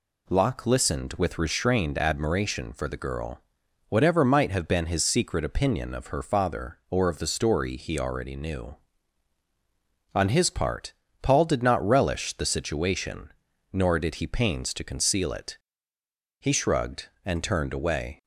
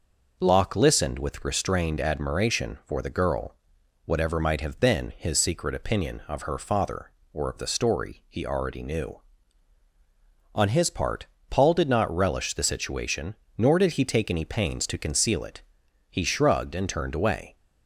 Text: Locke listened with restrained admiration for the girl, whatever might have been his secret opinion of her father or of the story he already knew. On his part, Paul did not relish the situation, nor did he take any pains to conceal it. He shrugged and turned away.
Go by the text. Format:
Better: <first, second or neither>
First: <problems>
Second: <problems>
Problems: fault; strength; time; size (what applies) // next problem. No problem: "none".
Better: second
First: skips "take any"; at 14.2 s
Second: none